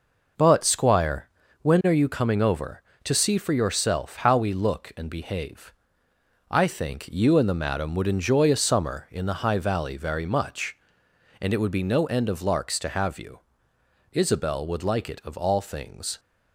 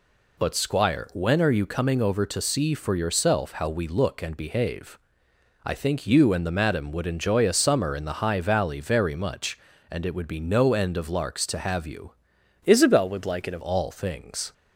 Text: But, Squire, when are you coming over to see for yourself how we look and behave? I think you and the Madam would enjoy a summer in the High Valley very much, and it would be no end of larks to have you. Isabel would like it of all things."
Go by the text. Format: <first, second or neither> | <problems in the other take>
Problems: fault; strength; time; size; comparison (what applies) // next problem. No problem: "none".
first | changes voice from "Isabel" to "of"; from 12.6 to 13.6 s; 1.0 s long